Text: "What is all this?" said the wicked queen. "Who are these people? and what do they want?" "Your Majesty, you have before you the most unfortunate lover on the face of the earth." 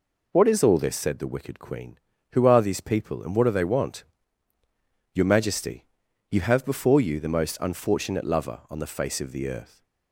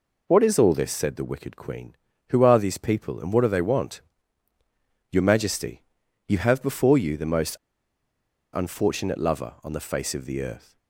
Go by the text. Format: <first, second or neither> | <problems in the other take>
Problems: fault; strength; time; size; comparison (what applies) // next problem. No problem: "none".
first | pauses between "most" and "unfortunate"; noticeable; at 7.5 s; 0.97 s long